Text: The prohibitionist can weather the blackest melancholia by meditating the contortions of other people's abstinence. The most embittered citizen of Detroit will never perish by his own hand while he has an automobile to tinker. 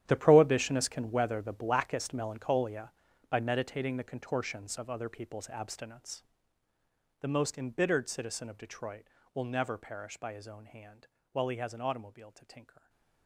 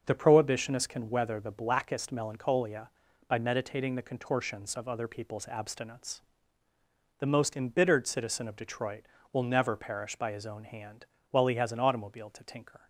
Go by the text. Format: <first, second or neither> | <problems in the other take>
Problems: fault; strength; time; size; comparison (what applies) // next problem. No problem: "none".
second | gets quieter; strong; throughout; 15.5 dB // starts louder than the rest; strong; until 1.0 s; 10.5 dB; noticeable in the second // pauses between "hand" and "while"; slight; at 11.0 s; 0.24 s long; slight in the second